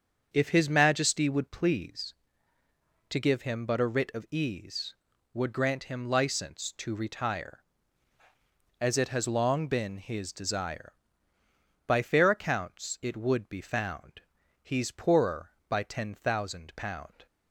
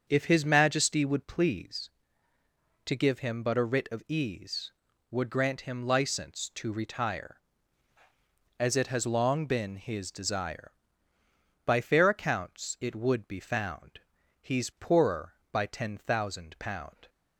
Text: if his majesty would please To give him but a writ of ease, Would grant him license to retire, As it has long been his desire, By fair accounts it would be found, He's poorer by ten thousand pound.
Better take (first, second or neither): neither